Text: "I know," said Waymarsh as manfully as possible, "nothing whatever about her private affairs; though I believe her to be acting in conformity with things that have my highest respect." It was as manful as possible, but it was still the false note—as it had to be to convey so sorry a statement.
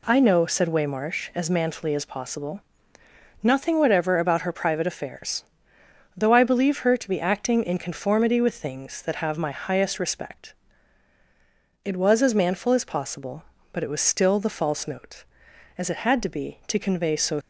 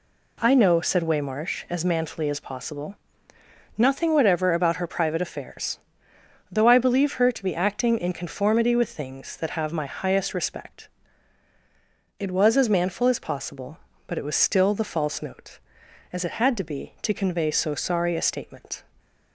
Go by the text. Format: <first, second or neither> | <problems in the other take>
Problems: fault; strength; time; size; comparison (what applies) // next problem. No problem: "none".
second | stops before "sorry a statement"; at 17.4 s